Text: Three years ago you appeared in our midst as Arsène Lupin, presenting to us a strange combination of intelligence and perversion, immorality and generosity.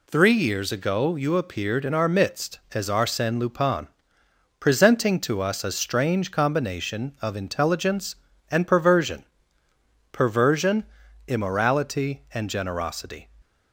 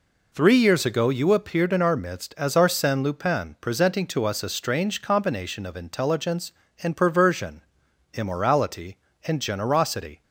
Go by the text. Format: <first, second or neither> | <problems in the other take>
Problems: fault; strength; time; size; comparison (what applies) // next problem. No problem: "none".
second | says "perversion" twice; at 10.1 s